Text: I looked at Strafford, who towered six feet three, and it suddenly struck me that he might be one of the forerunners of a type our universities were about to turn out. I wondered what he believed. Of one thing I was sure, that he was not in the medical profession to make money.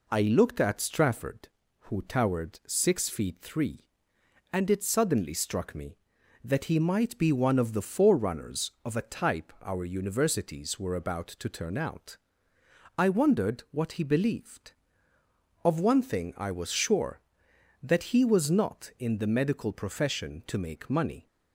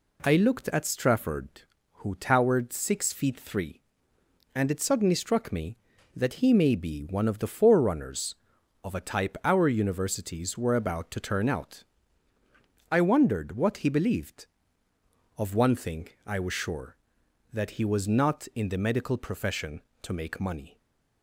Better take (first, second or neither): first